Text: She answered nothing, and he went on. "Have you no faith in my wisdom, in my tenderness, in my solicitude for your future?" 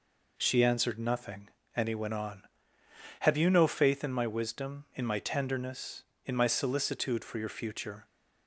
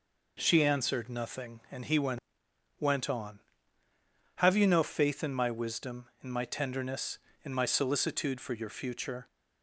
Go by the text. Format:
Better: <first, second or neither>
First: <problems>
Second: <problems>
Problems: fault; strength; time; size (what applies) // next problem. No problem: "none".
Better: first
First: none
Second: says "went" twice; at 2.7 s